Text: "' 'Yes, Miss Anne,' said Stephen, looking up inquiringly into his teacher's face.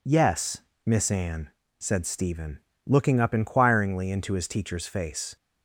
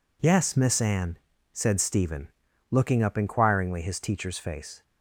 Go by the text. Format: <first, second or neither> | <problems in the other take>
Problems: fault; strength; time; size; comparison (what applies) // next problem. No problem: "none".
first | skips "into"; at 3.8 s